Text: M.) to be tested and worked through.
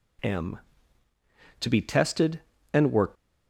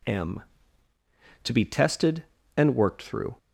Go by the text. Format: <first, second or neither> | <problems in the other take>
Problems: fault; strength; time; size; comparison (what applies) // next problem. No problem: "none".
second | stops before "through"; at 3.1 s